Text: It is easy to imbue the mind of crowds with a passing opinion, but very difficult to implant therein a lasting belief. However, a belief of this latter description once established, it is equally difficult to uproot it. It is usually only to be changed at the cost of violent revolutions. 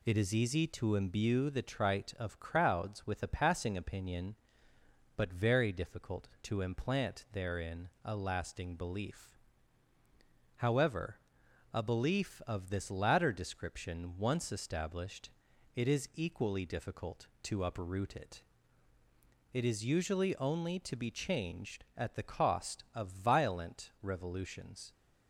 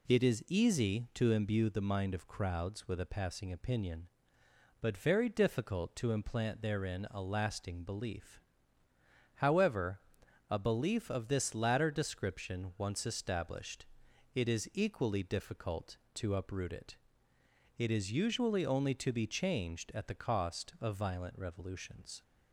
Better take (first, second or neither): second